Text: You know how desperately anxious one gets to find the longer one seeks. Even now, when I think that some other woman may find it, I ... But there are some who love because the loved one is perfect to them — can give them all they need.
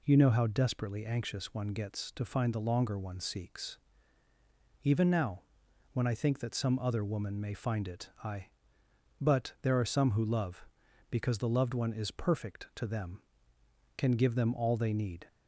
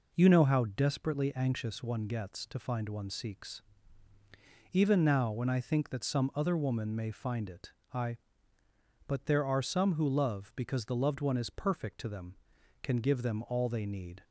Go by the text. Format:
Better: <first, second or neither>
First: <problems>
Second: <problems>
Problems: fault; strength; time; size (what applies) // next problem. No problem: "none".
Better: first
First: none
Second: skips "the longer"; at 2.8 s